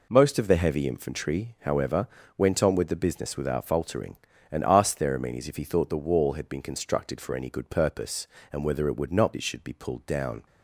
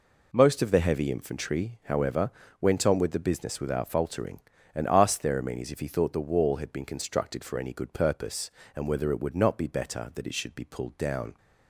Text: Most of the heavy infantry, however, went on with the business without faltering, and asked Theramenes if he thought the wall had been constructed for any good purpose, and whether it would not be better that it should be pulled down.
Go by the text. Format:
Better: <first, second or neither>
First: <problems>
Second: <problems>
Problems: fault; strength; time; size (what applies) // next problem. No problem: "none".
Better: second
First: skips "be better that"; at 9.3 s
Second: none